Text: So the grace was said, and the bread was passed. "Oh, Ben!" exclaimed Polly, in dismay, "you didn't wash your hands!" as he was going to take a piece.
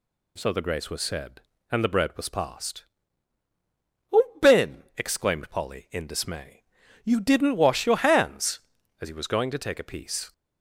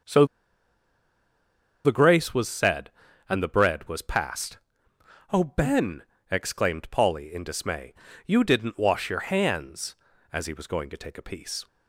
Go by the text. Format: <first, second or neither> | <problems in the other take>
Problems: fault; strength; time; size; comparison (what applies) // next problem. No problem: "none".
first | starts louder than the rest; until 2.6 s; 6.5 dB // pauses between "So" and "the"; strong; at 0.2 s; 1.5 s long